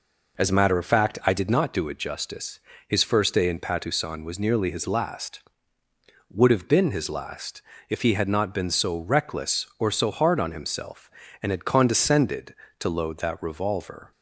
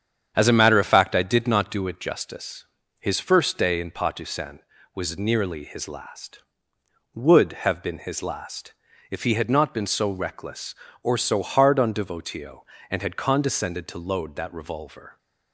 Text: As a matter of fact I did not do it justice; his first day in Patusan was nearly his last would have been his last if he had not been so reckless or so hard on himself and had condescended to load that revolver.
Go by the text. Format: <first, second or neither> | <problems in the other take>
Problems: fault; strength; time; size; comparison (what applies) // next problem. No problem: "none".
first | starts louder than the rest; strong; until 1.3 s; 8.5 dB // pauses between "last" and "if"; at 8.7 s; 0.38 s long; slight in the first // says "devotio" for "himself"; at 11.9 s